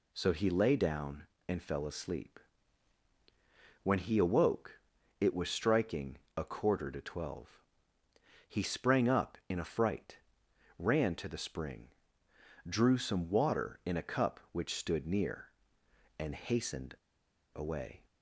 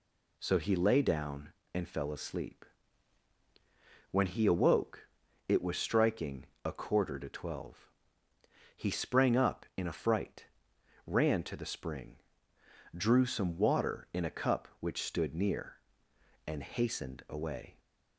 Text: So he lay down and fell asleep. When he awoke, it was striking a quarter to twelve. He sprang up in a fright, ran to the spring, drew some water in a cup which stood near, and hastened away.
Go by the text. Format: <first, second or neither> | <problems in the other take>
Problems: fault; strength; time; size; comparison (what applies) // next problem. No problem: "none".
second | pauses between "striking" and "a"; slight; at 6.1 s; 0.18 s long; slight in the second // pauses between "hastened" and "away"; noticeable; at 16.9 s; 0.58 s long